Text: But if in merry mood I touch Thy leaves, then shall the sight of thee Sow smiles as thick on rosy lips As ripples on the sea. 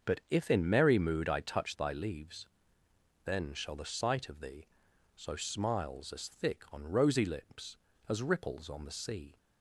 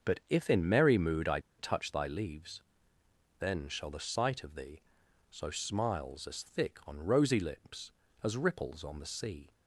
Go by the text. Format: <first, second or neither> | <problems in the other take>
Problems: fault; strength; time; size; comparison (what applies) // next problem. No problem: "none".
first | starts louder than the rest; until 1.1 s; 6.5 dB; also in the first // pauses between "I" and "touch"; slight; at 1.3 s; 0.19 s long // pauses between "thee" and "Sow"; noticeable; at 4.8 s; 0.48 s long; noticeable in the first